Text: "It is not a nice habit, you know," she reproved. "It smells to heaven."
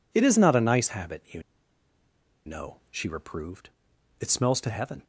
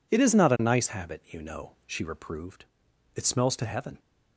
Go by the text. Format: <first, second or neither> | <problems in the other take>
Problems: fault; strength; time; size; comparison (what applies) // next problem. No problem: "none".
second | pauses between "you" and "know"; at 1.4 s; 1.0 s long